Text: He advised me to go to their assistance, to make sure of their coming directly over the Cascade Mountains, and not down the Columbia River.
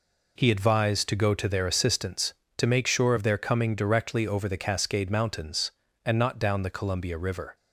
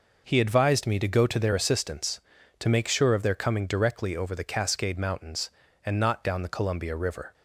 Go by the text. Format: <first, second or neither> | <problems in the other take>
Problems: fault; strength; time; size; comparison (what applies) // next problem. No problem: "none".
second | skips "me"; at 1.0 s